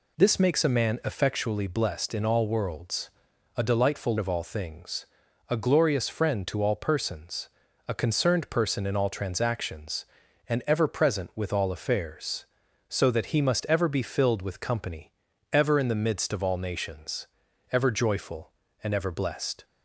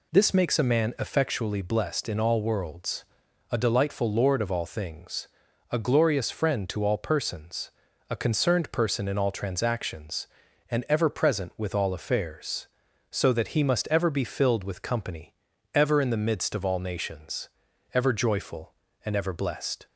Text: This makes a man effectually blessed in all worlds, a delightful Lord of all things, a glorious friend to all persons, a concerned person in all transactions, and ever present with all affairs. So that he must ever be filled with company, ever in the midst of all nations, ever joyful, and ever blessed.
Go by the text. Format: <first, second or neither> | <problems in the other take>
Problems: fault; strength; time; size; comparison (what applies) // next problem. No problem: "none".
second | skips "Lord"; at 4.1 s